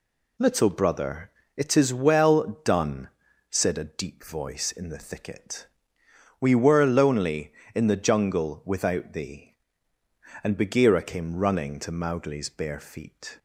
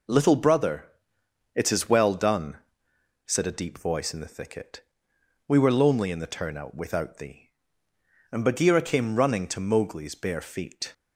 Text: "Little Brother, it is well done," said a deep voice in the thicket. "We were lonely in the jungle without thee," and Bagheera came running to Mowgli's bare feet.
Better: first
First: none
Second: says "turnout" for "jungle"; at 6.2 s

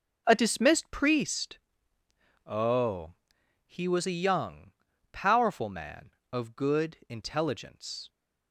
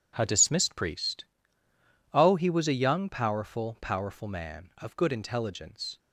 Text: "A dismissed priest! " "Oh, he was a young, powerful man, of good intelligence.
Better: first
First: none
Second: starts louder than the rest; strong; until 1.1 s; 8 dB // says "powerful" twice; at 3.8 s

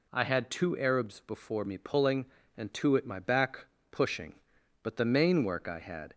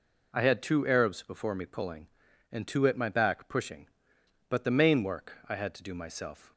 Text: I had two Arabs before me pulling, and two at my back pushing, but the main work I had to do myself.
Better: second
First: pauses between "back" and "pushing"; slight; at 3.6 s; 0.24 s long // stops before "to do myself"; at 6.1 s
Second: none

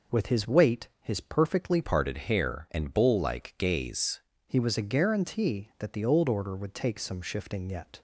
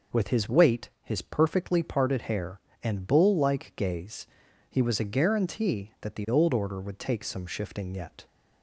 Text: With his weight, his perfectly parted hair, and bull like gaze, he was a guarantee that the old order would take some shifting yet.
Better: second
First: changes voice from "parted" to "gaze"; from 1.8 to 4.1 s; 2.3 s long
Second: none

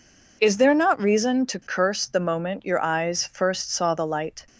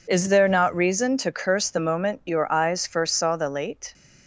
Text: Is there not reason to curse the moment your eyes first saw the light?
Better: first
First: none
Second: says "late" for "light"; at 3.4 s

